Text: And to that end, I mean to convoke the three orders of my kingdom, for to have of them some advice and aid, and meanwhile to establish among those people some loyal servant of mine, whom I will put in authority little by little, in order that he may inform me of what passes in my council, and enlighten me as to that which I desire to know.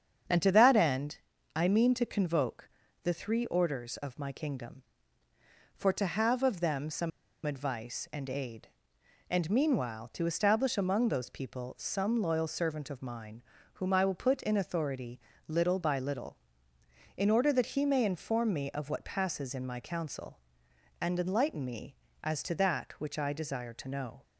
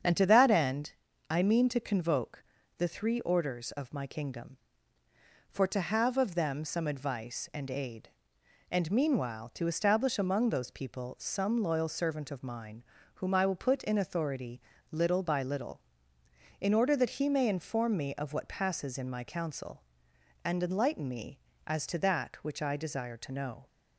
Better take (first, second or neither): second